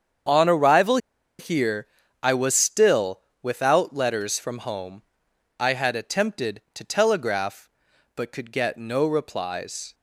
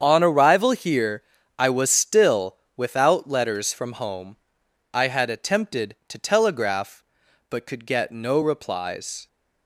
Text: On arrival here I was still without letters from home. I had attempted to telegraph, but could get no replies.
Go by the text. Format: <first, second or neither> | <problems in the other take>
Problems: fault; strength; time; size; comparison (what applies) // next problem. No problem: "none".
second | starts louder than the rest; strong; until 1.6 s; 7.5 dB; strong in the second // pauses between "arrival" and "here"; at 0.9 s; 0.41 s long // pauses between "here" and "I"; at 1.8 s; 0.38 s long; also in the second // pauses between "still" and "without"; slight; at 3.1 s; 0.20 s long; slight in the second